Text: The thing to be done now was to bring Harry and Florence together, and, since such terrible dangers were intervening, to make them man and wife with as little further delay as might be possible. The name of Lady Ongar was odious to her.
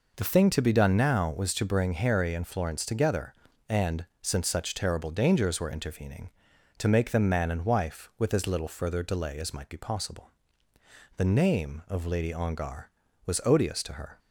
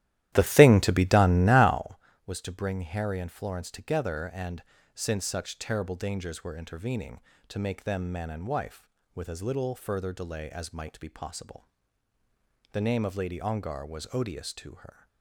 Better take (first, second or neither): first